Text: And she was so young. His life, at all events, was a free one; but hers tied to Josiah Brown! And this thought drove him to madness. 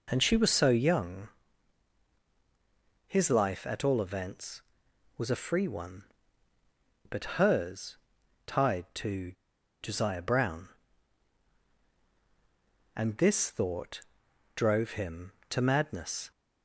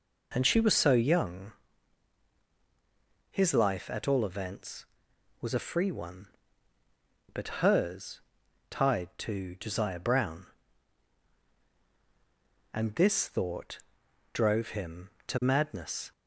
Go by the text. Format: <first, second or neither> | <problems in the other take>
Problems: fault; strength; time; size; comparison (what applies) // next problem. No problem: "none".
second | pauses between "hers" and "tied"; noticeable; at 7.9 s; 0.50 s long; noticeable in the second // pauses between "to" and "Josiah"; noticeable; at 9.3 s; 0.49 s long // pauses between "thought" and "drove"; noticeable; at 14.0 s; 0.52 s long; noticeable in the second